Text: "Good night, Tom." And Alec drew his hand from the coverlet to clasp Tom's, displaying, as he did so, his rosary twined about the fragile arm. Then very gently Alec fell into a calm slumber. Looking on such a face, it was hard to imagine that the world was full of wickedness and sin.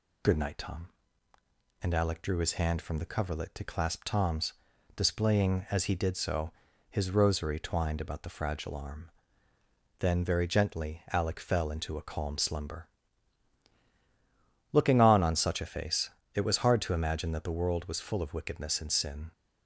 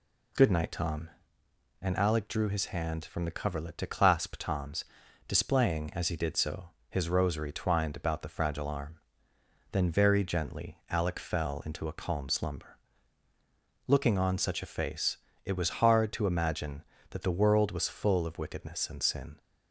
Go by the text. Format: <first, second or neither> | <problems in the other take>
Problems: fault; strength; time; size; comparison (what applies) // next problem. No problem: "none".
second | says "on" twice; at 15.2 s